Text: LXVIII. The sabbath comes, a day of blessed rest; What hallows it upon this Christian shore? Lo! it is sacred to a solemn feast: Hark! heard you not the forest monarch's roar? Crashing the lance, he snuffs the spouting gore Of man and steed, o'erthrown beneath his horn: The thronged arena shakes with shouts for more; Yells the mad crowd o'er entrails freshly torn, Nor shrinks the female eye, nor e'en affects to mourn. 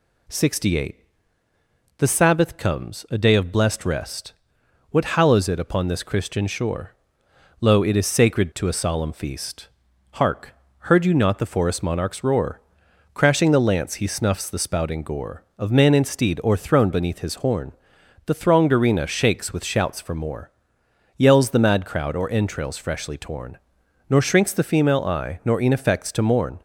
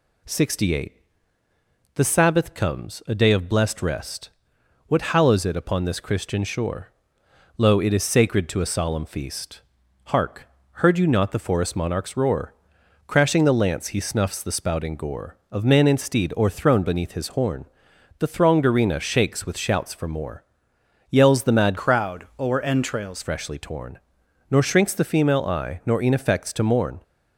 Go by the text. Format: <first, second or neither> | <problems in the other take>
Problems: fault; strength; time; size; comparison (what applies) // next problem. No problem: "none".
first | changes voice from "crowd" to "entrails"; from 21.7 to 23.2 s; 1.5 s long